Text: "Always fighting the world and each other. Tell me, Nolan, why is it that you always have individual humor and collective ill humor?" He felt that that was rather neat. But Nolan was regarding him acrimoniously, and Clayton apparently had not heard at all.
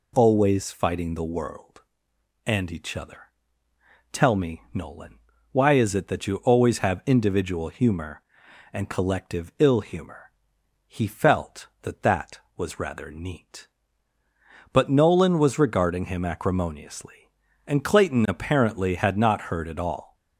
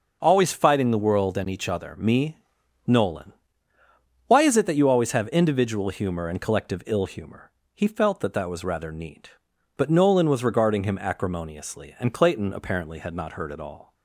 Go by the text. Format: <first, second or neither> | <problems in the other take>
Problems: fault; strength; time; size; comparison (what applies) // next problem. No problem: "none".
first | skips "Tell"; at 1.9 s